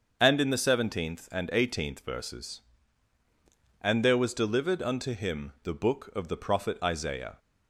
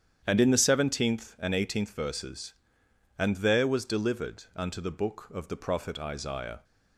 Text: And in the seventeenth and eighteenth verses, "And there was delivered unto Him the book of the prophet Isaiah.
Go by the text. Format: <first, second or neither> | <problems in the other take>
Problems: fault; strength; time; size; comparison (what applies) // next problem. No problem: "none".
first | starts louder than the rest; strong; until 1.2 s; 9 dB; also in the first // skips "Him"; at 4.7 s